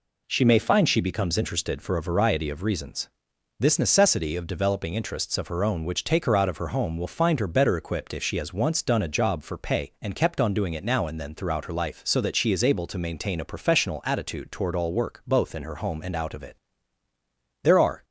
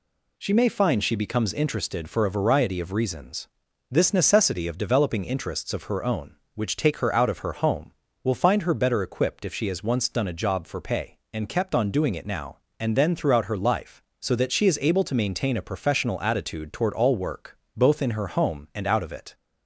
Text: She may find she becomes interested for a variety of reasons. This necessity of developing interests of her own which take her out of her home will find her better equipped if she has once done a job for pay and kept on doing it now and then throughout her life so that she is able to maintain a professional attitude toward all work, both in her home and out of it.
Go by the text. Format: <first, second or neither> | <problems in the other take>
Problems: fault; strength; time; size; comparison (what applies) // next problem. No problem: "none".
second | goes on to say "There are"; slight; from 17.6 s on; 0.42 s long